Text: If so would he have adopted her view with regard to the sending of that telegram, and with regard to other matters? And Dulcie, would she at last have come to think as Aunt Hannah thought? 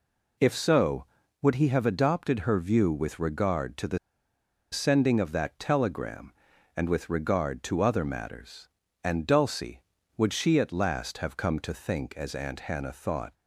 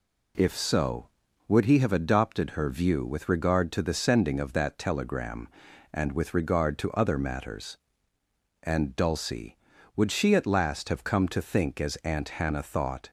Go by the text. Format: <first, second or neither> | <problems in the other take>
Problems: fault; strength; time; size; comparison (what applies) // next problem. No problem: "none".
second | pauses between "the" and "sending"; noticeable; at 3.9 s; 0.74 s long